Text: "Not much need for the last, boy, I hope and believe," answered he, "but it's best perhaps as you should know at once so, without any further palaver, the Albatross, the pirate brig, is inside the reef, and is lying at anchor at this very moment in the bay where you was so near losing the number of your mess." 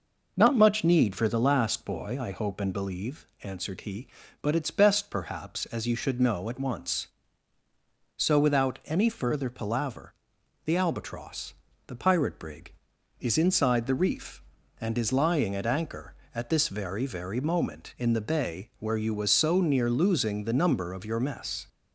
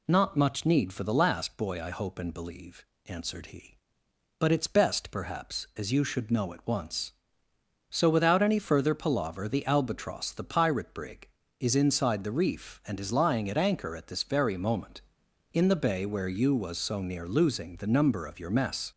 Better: second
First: says "very" twice; at 17.0 s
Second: none

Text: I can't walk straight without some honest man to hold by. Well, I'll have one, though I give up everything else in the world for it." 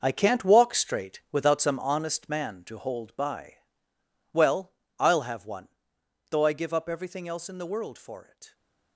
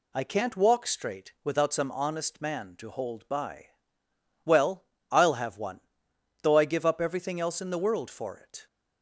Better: second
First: gets quieter; strong; throughout; 12 dB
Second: none

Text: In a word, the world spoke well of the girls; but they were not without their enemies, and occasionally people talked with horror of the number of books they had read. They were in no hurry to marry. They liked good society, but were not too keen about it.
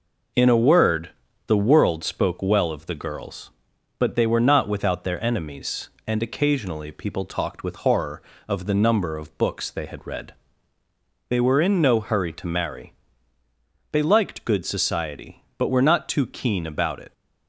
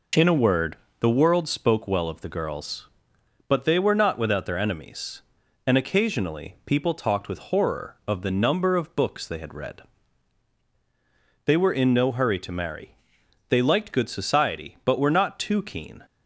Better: first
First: none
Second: stops before "about it"; at 16.0 s

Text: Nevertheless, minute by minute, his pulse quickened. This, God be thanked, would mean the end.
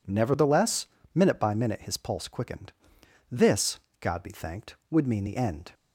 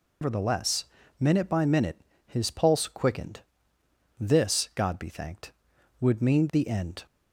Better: first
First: none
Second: loses the start of "Nevertheless"; at 0.2 s; 145 ms

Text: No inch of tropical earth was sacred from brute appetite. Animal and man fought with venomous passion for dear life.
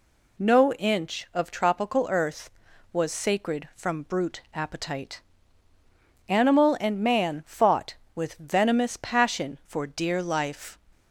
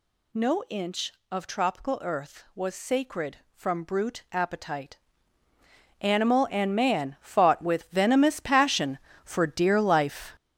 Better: first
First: none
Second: gets louder; strong; throughout; 8 dB

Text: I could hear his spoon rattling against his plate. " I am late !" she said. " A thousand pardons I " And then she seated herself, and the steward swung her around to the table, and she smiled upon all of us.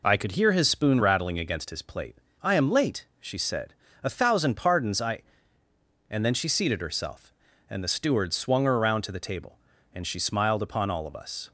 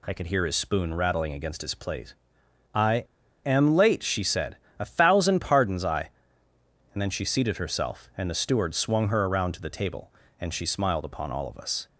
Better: first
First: none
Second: pauses between "I" and "am"; at 3.0 s; 0.41 s long

